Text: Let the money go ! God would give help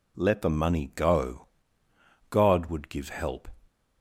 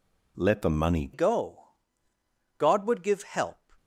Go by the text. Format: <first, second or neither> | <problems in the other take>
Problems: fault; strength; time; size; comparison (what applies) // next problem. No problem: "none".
first | changes voice at "go"; from 1.1 s on; 2.6 s long